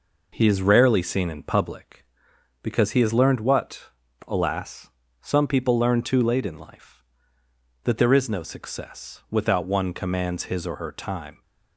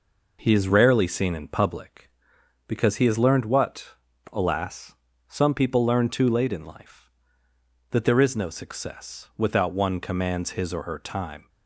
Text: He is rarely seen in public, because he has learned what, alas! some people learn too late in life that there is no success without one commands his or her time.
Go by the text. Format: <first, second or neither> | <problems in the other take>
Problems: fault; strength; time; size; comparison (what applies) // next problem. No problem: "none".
neither | none